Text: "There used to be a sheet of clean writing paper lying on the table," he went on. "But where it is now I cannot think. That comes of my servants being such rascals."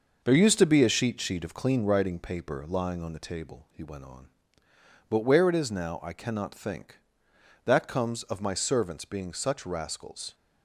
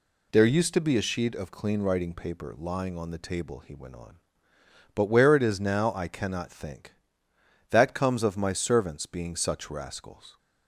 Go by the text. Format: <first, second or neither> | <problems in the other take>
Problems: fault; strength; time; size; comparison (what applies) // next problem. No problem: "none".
second | says "sheet" twice; at 1.2 s